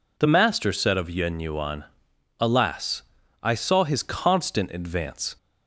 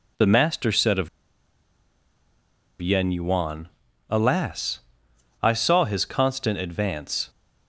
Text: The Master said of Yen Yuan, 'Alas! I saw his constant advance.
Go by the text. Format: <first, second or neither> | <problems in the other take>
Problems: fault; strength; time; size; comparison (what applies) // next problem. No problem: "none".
first | pauses between "of" and "Yen"; strong; at 1.0 s; 1.7 s long